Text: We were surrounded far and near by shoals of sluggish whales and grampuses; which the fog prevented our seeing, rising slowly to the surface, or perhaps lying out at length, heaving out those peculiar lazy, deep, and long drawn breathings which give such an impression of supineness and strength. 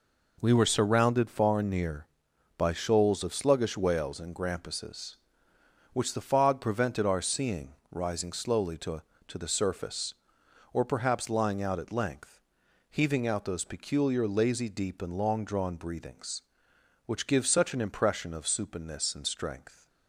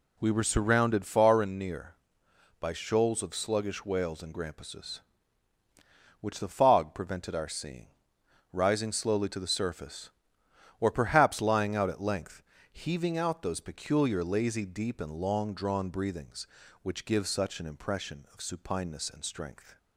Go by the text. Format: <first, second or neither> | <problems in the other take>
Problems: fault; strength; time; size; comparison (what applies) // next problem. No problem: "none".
second | says "to" twice; at 9.2 s